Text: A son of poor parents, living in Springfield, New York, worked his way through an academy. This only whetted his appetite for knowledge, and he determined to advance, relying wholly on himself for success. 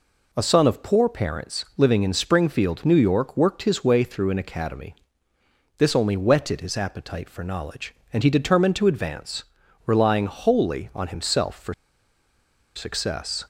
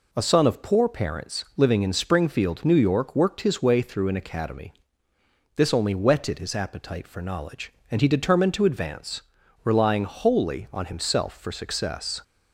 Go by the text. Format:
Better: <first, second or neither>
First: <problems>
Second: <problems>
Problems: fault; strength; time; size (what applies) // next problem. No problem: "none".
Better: second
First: pauses between "for" and "success"; at 11.7 s; 1.0 s long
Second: none